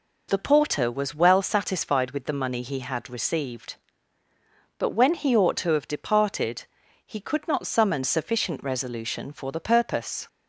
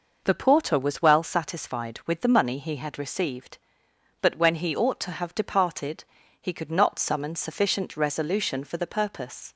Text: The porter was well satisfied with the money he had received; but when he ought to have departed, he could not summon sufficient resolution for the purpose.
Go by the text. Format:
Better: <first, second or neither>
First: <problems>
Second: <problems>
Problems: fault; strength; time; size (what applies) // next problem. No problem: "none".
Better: neither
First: none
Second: none